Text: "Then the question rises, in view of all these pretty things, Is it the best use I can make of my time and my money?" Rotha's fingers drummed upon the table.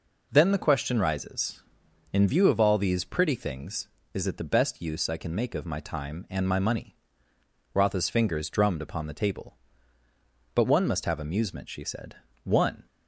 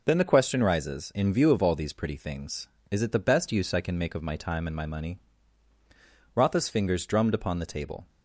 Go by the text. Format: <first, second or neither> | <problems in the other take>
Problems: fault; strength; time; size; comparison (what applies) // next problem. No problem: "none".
second | goes on to say "But one must have amusement she said One"; strong; from 10.5 s on; 2.3 s long